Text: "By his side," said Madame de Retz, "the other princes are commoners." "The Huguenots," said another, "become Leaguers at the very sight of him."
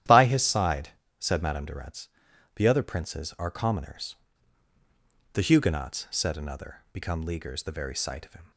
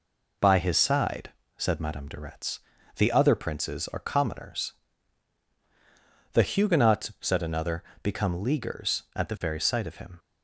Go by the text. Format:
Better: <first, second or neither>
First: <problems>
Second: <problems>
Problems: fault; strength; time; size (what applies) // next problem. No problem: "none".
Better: second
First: starts louder than the rest; strong; until 1.3 s; 11.5 dB // skips "at"; at 7.6 s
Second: none